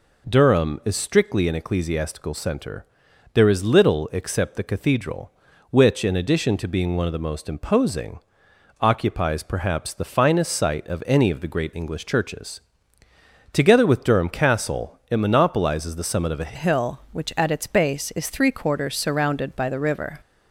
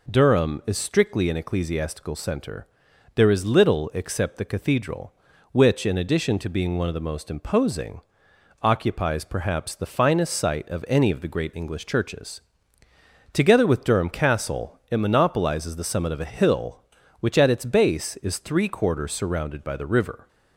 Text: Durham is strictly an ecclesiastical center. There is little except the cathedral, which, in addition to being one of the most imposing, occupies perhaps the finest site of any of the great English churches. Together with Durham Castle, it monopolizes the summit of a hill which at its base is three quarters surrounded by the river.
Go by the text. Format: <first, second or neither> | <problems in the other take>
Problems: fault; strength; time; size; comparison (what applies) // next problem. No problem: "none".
second | changes voice at "hill"; from 16.5 s on; 3.7 s long